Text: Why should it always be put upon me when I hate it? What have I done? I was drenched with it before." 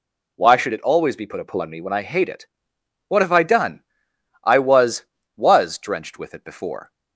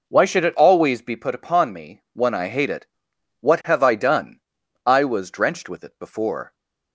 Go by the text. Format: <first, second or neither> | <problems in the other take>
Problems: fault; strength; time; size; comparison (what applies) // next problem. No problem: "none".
second | says "was" twice; at 5.3 s